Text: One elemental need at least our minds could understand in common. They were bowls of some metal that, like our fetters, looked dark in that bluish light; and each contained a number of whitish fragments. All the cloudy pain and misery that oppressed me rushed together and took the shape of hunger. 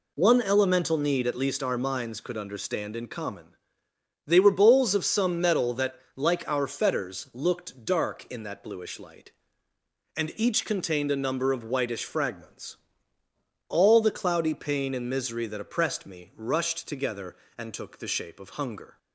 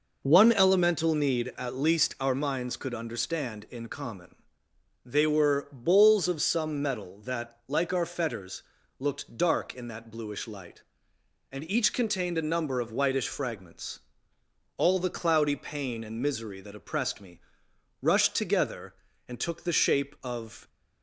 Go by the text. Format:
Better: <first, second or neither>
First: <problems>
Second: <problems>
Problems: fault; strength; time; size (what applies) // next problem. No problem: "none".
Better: first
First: none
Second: pauses between "me" and "rushed"; noticeable; at 17.4 s; 0.60 s long // stops before "hunger"; at 20.6 s